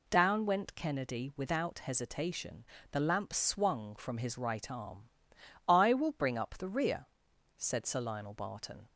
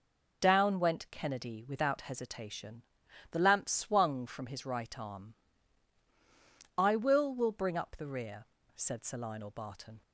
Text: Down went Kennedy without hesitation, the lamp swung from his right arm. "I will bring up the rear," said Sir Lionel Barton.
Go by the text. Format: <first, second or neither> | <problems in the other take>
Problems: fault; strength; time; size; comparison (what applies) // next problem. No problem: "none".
first | says "will" twice; at 7.3 s